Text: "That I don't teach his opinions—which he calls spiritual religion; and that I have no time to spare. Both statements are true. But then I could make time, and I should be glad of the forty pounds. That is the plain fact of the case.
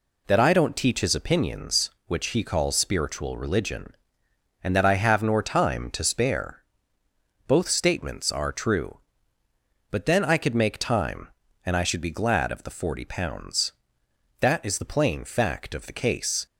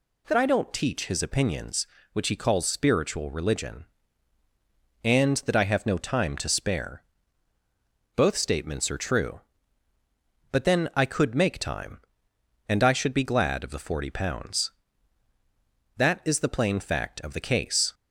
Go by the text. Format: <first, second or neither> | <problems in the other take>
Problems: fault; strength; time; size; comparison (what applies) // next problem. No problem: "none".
second | says "nor" for "no"; at 5.2 s